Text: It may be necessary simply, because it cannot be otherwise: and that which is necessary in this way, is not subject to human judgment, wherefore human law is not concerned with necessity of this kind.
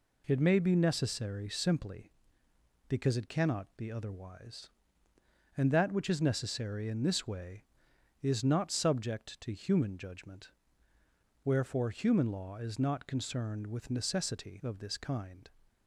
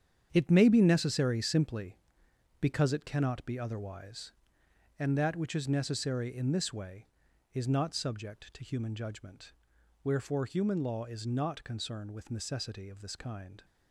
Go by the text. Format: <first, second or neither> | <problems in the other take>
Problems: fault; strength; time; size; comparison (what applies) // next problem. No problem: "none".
first | gets quieter; strong; throughout; 10.5 dB